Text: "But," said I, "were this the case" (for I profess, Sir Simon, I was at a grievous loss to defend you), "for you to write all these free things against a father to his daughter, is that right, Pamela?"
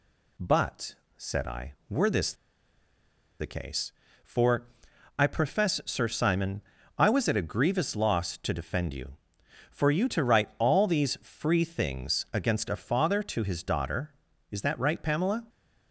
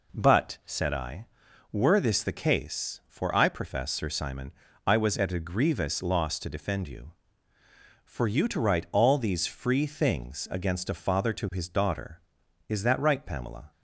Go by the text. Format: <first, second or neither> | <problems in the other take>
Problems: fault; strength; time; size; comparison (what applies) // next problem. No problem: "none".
second | pauses between "this" and "the"; at 2.3 s; 1.0 s long // pauses between "for" and "I"; noticeable; at 4.6 s; 0.50 s long